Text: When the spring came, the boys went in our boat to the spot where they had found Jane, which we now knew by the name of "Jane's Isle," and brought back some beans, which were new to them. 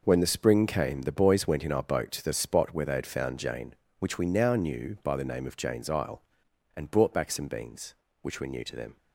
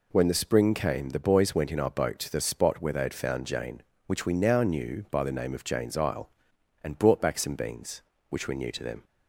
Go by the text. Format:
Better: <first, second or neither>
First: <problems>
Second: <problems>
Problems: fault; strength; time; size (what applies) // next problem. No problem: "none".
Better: second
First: gets quieter; strong; throughout; 10.5 dB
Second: none